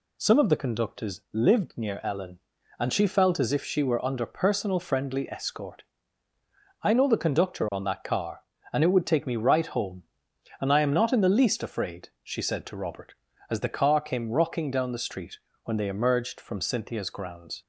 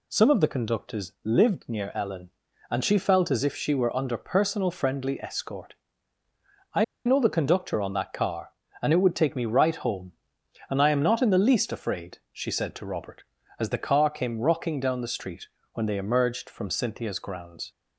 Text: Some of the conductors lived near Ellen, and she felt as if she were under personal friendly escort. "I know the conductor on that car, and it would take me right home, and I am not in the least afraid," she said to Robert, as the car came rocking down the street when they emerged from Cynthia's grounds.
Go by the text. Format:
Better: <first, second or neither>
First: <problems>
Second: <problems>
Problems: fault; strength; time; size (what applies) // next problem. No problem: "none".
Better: first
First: pauses between "street" and "when"; slight; at 15.3 s; 0.28 s long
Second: pauses between "I" and "know"; slight; at 6.8 s; 0.22 s long // pauses between "street" and "when"; slight; at 15.4 s; 0.28 s long